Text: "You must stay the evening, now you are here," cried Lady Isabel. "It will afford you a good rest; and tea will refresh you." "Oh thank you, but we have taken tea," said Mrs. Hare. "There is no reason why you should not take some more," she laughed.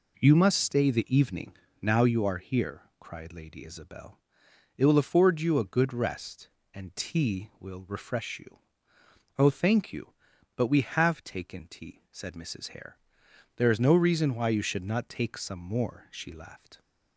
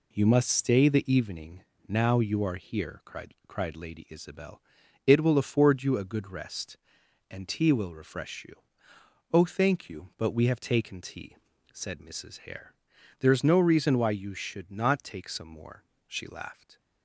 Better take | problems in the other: first | says "cried" twice; at 3.4 s

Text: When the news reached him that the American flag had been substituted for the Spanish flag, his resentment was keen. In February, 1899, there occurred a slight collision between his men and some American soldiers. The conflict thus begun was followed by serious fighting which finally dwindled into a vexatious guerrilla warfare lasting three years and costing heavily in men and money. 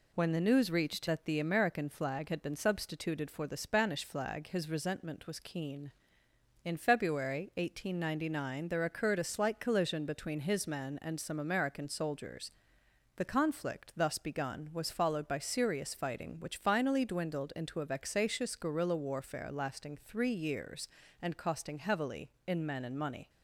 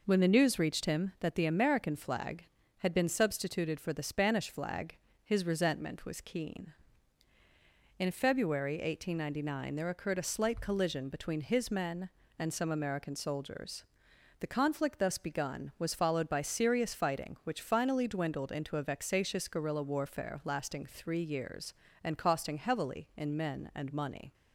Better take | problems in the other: second | skips "him"; at 1.0 s

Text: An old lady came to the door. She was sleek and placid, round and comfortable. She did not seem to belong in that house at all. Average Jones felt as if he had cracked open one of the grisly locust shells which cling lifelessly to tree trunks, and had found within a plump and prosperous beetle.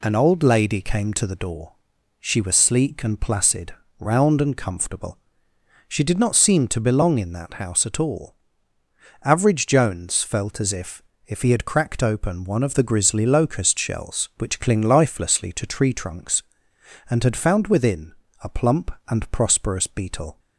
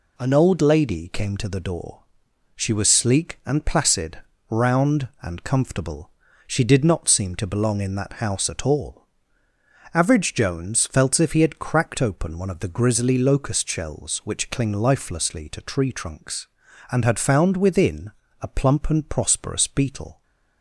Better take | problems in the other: second | says "if" twice; at 11.2 s // pauses between "within" and "a"; slight; at 18.1 s; 0.30 s long; slight in the second

